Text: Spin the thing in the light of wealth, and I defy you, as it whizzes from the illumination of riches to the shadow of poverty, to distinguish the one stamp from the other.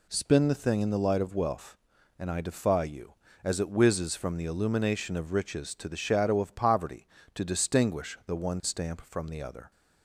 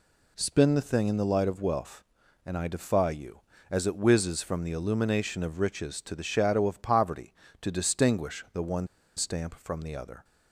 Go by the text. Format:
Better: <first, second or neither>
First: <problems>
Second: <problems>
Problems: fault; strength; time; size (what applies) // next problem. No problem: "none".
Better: first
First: none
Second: pauses between "one" and "stamp"; slight; at 8.8 s; 0.30 s long